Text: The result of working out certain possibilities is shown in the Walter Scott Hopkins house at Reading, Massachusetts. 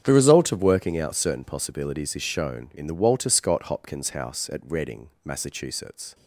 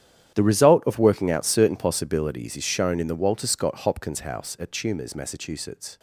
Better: first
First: starts louder than the rest; strong; until 1.0 s; 8.5 dB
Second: starts louder than the rest; strong; until 1.3 s; 10.5 dB // says "Tumors" for "Reading"; at 4.7 s

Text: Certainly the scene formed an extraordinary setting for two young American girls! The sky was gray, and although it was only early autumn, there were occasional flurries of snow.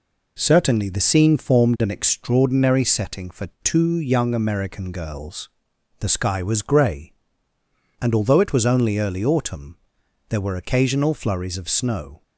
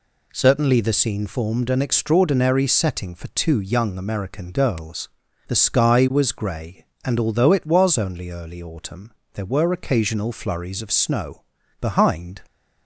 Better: first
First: none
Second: goes on to say "Behind"; from 11.8 s on; 0.60 s long

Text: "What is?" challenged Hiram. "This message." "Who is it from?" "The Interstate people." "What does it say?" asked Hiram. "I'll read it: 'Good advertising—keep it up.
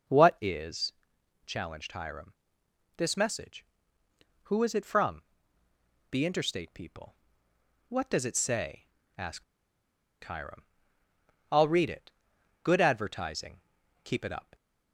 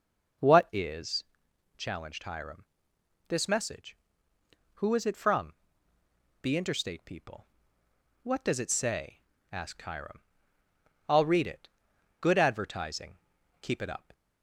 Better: second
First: pauses between "asked" and "Hiram"; noticeable; at 9.4 s; 0.81 s long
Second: none

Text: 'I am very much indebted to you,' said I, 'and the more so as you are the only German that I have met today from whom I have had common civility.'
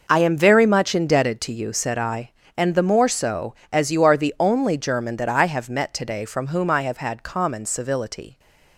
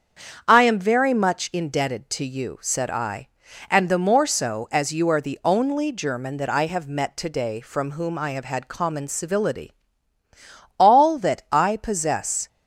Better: first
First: none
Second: starts louder than the rest; strong; until 1.5 s; 7.5 dB // goes on to say "All that I possess"; strong; from 10.7 s on; 1.7 s long

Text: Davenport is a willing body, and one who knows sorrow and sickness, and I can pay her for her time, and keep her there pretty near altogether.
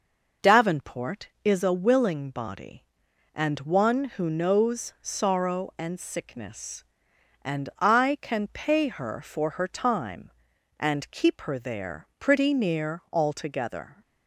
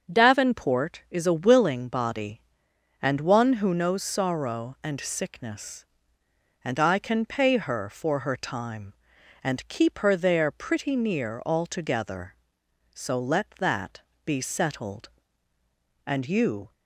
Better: first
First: none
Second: starts louder than the rest; until 1.1 s; 6.5 dB // goes on to say "So let that be settled And you"; strong; from 12.9 s on; 3.7 s long

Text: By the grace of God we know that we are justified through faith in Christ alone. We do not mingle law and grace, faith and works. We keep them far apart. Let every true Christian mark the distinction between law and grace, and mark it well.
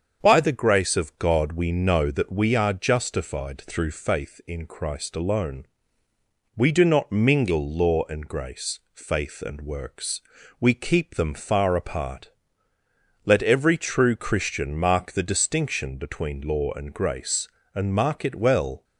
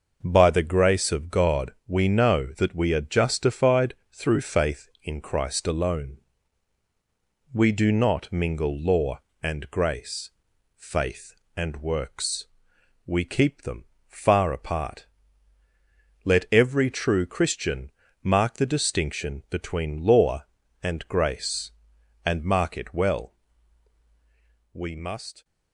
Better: first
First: starts louder than the rest; strong; until 1.2 s; 7 dB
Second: starts louder than the rest; noticeable; until 1.2 s; 6 dB // pauses between "God" and "we"; slight; at 1.7 s; 0.16 s long // pauses between "justified" and "through"; slight; at 3.9 s; 0.18 s long // pauses between "them" and "far"; slight; at 13.8 s; 0.24 s long // pauses between "Christian" and "mark"; slight; at 17.9 s; 0.32 s long // goes on to say "We must"; noticeable; from 24.7 s on; 0.70 s long

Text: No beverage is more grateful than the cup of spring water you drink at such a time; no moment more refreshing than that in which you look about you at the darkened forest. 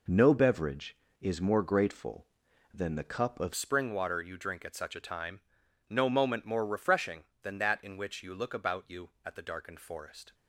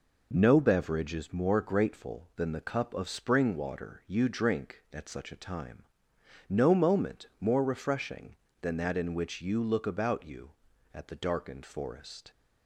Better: second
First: changes voice at "spring"; from 3.5 s on; 6.8 s long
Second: none

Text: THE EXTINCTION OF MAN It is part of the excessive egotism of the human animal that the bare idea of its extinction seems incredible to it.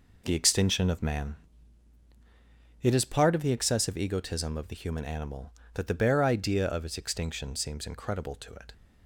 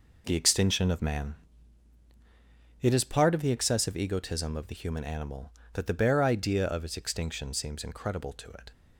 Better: neither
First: pauses between "MAN" and "It"; strong; at 1.3 s; 1.4 s long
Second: pauses between "MAN" and "It"; strong; at 1.3 s; 1.4 s long

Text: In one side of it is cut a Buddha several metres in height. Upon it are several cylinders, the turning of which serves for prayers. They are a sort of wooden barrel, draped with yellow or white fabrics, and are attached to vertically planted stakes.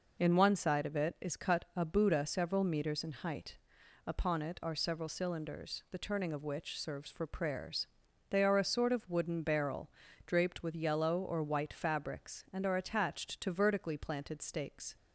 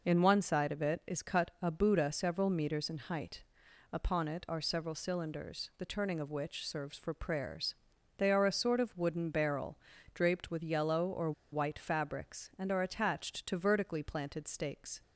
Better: first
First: none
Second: pauses between "or" and "white"; slight; at 11.3 s; 0.20 s long

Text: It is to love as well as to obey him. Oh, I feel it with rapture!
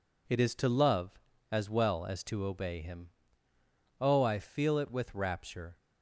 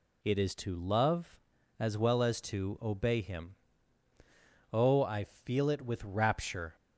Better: neither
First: none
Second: none

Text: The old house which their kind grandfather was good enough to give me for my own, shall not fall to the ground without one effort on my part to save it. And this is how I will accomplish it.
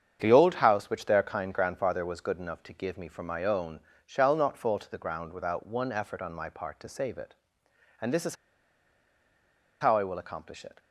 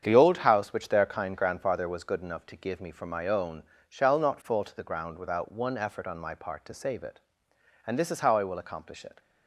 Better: second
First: starts louder than the rest; strong; until 1.2 s; 8 dB // pauses between "is" and "how"; strong; at 8.3 s; 1.4 s long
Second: starts louder than the rest; strong; until 1.0 s; 8 dB

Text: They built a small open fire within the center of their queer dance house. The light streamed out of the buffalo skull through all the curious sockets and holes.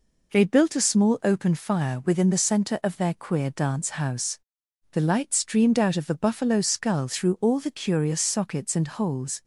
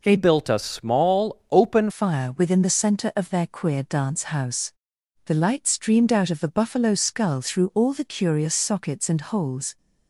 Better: first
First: none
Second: changes voice from "built" to "open"; from 0.1 to 1.8 s; 1.7 s long

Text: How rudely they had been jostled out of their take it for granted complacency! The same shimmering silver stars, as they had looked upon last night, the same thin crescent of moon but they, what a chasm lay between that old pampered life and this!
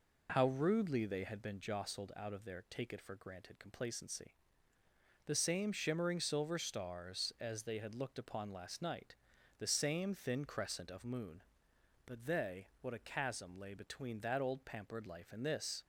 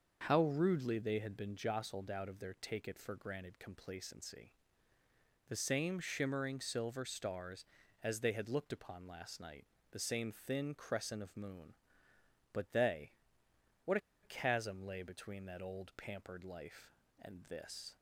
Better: first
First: none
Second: starts louder than the rest; until 1.2 s; 6.5 dB // pauses between "what" and "a"; slight; at 13.9 s; 0.24 s long

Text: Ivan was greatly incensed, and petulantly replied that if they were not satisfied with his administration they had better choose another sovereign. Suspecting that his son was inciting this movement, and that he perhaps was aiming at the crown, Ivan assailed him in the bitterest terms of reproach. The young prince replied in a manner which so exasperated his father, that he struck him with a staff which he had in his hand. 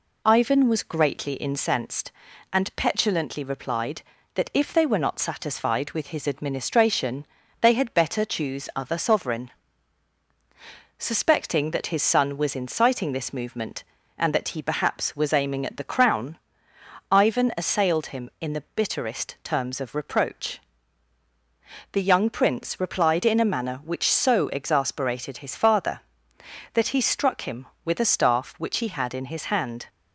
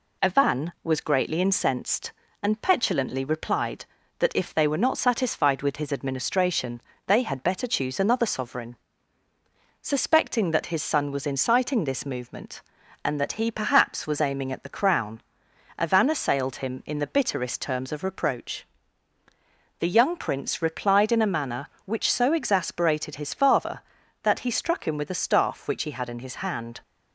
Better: second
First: pauses between "administration" and "they"; at 7.2 s; 0.38 s long // says "other" for "another"; at 8.7 s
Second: pauses between "administration" and "they"; slight; at 6.8 s; 0.26 s long

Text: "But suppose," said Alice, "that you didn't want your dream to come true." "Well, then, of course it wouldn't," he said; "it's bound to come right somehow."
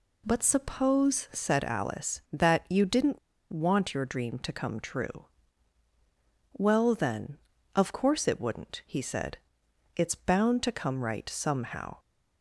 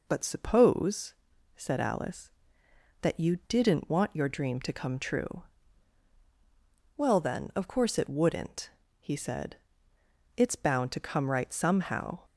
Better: second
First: pauses between "didn't" and "want"; slight; at 3.1 s; 0.33 s long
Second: none

